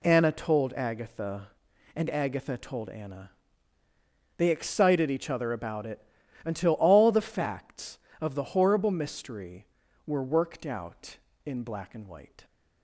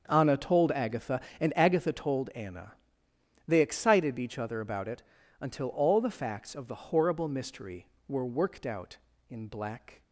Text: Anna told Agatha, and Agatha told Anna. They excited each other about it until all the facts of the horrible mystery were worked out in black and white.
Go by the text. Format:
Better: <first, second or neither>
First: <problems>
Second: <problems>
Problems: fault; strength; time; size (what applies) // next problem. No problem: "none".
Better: first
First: pauses between "it" and "until"; at 6.0 s; 0.44 s long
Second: starts louder than the rest; until 1.1 s; 7 dB // pauses between "it" and "until"; at 5.0 s; 0.38 s long // stops before "and white"; at 10.0 s